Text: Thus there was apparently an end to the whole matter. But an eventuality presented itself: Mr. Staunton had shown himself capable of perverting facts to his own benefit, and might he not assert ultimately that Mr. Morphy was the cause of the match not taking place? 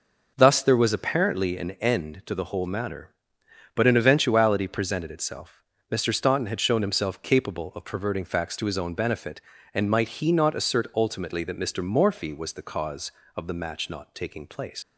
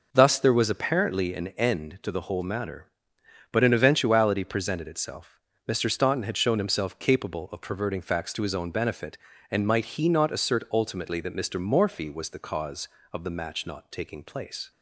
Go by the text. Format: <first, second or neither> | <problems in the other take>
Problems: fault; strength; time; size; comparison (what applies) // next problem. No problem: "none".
second | leaves "place" unfinished; at 14.8 s; 110 ms